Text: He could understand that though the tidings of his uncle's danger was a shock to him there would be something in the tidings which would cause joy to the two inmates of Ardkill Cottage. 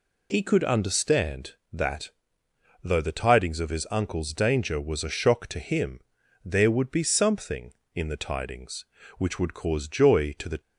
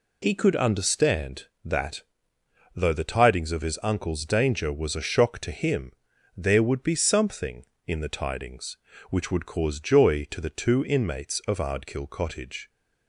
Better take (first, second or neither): second